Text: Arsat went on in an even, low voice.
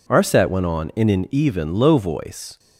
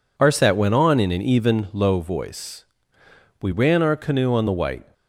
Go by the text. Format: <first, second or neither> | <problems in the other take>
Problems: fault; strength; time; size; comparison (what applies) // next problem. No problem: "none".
first | goes on to say "We ran our canoe on the white"; from 3.4 s on; 1.5 s long